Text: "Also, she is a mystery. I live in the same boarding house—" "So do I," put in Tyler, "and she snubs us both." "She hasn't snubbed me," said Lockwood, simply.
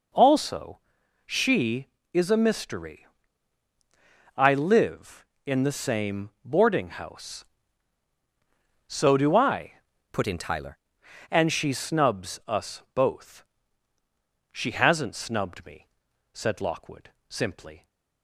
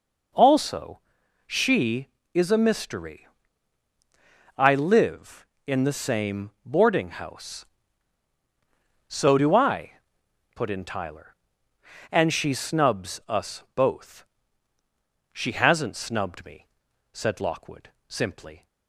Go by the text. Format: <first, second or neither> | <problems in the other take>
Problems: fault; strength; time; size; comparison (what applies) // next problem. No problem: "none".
second | pauses between "same" and "boarding"; slight; at 6.2 s; 0.16 s long; slight in the second // changes voice from "put" to "Tyler"; from 10.1 to 10.7 s; 0.6 s long